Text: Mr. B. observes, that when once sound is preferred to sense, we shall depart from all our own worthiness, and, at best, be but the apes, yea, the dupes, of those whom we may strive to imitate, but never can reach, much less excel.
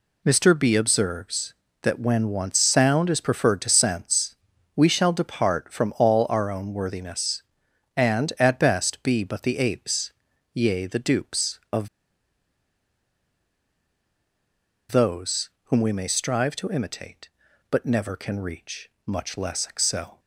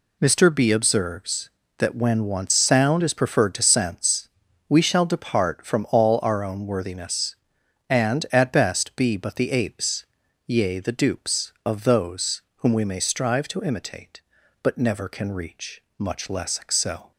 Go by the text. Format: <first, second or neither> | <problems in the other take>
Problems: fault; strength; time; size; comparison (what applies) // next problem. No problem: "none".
second | pauses between "of" and "those"; strong; at 11.8 s; 3.0 s long // pauses between "those" and "whom"; slight; at 15.4 s; 0.16 s long; slight in the second